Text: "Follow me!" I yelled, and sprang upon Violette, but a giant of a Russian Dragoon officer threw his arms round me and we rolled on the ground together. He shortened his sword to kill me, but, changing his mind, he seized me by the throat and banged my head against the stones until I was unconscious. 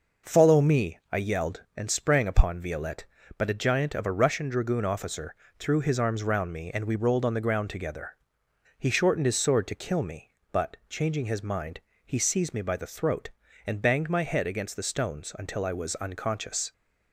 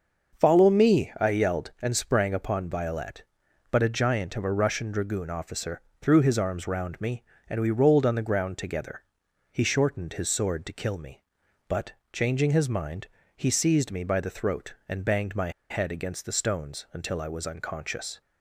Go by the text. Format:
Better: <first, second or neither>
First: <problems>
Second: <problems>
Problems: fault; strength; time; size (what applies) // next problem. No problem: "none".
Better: first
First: pauses between "officer" and "threw"; slight; at 5.3 s; 0.24 s long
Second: starts louder than the rest; until 1.4 s; 6.5 dB // pauses between "officer" and "threw"; slight; at 5.8 s; 0.20 s long // pauses between "my" and "head"; slight; at 15.5 s; 0.19 s long